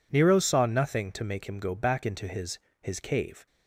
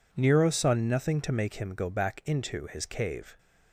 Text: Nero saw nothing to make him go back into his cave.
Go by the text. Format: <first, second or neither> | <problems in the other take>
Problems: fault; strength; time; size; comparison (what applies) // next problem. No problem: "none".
second | says "his" twice; at 2.8 s